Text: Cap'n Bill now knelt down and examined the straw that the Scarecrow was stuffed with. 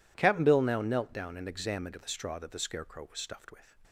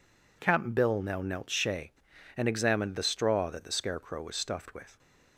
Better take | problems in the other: first | says "shay" for "down"; at 1.4 s

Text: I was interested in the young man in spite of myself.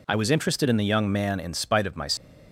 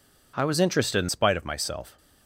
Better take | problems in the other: first | skips "the young man in"; at 1.0 s

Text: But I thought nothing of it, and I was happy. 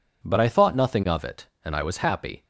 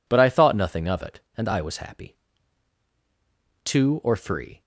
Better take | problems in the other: first | goes on to say "Two or three"; noticeable; from 3.6 s on; 0.98 s long

